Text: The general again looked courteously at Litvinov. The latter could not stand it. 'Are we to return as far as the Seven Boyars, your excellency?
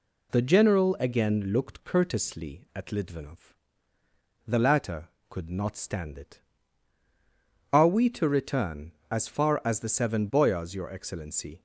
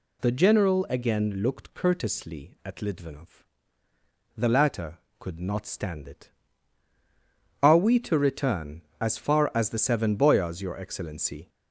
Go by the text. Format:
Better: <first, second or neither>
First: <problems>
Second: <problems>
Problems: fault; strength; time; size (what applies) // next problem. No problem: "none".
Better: first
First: none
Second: gets louder; slight; throughout; 2.5 dB